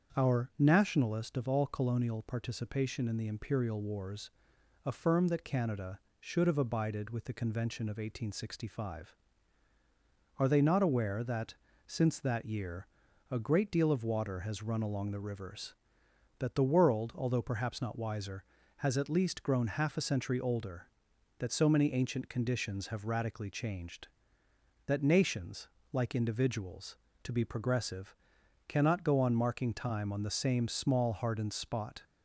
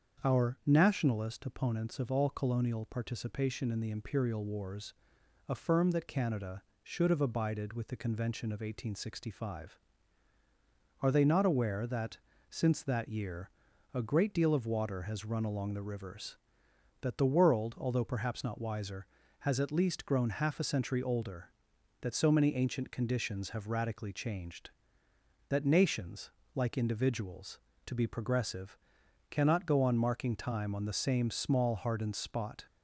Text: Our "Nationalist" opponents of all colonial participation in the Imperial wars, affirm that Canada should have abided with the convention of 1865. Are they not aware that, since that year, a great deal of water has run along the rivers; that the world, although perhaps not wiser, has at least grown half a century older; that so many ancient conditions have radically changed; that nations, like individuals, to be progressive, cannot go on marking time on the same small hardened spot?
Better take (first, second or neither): second